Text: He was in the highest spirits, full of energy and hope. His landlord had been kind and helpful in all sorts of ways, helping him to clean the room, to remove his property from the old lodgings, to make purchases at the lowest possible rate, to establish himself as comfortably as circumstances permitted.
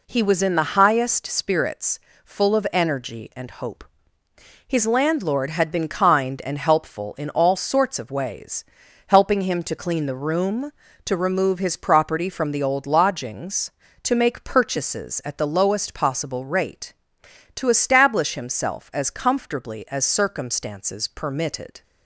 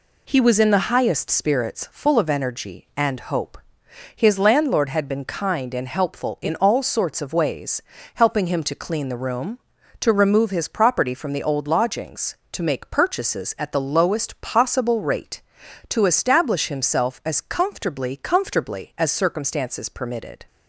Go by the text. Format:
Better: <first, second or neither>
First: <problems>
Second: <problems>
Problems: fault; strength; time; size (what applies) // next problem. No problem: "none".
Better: first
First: none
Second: says "comfortably" twice; at 18.1 s